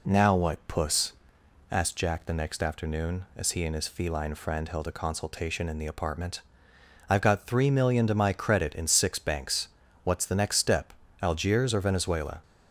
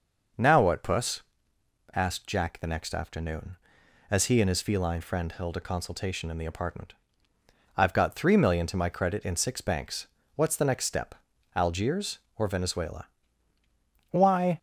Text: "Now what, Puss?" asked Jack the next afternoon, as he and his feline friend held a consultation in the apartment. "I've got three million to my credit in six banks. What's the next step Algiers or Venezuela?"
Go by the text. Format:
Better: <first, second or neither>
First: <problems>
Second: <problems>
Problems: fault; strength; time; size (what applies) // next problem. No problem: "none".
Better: first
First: pauses between "step" and "Algiers"; slight; at 10.9 s; 0.30 s long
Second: pauses between "step" and "Algiers"; at 11.1 s; 0.40 s long // goes on to say "Why"; slight; from 14.0 s on; 0.48 s long